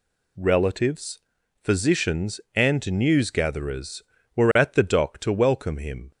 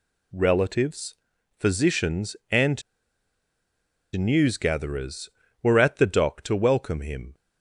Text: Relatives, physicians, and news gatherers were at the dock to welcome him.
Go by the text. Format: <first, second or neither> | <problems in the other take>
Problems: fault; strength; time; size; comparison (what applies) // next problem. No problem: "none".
first | pauses between "and" and "news"; strong; at 2.8 s; 1.3 s long